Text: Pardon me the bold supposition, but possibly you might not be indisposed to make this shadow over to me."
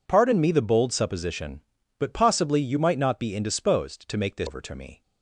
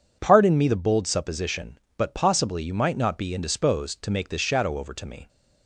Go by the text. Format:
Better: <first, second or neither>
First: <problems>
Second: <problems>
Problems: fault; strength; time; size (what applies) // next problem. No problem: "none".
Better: second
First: skips "shadow"; at 4.4 s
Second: none